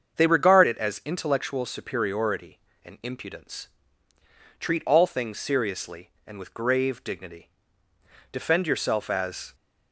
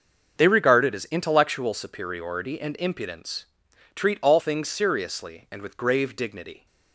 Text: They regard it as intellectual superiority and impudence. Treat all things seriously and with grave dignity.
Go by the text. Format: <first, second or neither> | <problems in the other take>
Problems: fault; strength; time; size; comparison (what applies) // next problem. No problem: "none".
second | starts louder than the rest; until 1.2 s; 7 dB; noticeable in the second // goes on to say "Defend yourself as"; noticeable; from 8.3 s on; 1.2 s long